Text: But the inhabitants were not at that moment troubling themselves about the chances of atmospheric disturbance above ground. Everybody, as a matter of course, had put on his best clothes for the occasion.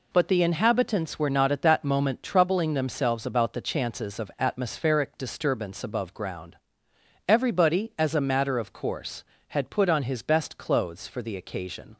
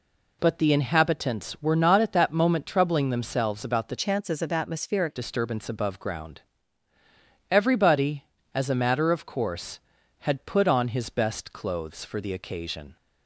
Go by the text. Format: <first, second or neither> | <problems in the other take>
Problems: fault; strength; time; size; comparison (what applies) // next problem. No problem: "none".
first | changes voice from "chances" to "atmospheric"; from 3.9 to 5.1 s; 1.2 s long